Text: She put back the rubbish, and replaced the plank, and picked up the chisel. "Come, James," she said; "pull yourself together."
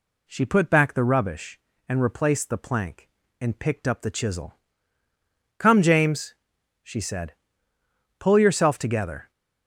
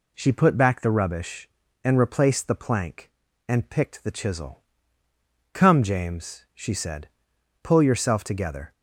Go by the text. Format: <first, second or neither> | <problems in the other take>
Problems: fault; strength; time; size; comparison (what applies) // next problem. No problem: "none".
first | skips "up"; at 4.0 s